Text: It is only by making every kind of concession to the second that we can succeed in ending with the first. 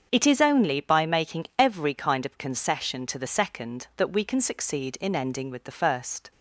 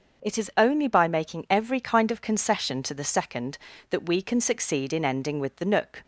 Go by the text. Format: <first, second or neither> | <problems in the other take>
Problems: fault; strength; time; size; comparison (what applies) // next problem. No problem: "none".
first | starts louder than the rest; until 1.3 s; 6 dB; strong in the first // says "nook" for "first"; at 5.6 s